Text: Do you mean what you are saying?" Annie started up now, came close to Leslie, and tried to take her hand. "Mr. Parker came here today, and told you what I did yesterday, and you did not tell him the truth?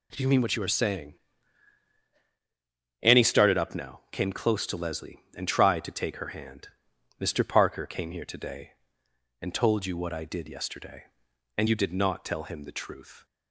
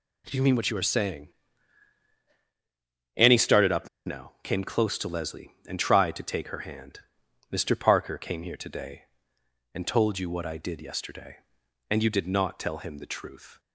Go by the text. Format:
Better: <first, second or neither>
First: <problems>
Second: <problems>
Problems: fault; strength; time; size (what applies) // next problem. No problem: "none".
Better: first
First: none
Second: pauses between "up" and "now"; slight; at 3.8 s; 0.17 s long